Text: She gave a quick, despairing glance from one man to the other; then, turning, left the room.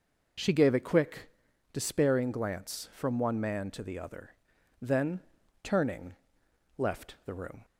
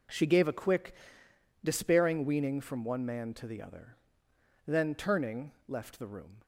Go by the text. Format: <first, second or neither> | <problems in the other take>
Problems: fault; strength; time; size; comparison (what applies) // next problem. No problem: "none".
first | says "weaning" for "glance"; at 2.2 s